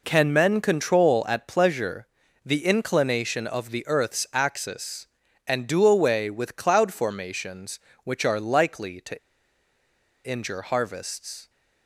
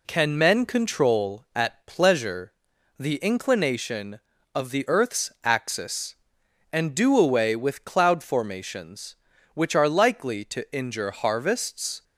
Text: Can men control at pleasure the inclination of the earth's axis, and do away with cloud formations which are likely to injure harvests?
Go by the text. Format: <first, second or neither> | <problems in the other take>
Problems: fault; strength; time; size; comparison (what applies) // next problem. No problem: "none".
second | pauses between "pleasure" and "the"; at 2.0 s; 0.38 s long; noticeable in the second // pauses between "to" and "injure"; at 9.1 s; 1.0 s long